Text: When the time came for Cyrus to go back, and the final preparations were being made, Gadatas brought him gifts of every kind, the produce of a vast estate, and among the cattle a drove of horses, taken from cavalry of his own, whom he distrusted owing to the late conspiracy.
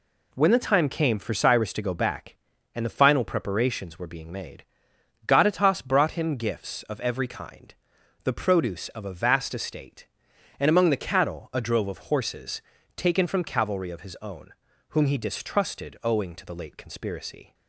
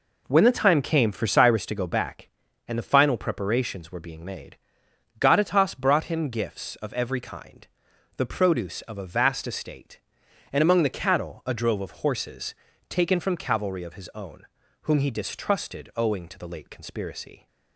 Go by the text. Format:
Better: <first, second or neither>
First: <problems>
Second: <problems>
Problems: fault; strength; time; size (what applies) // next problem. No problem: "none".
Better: first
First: none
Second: starts louder than the rest; until 1.7 s; 4 dB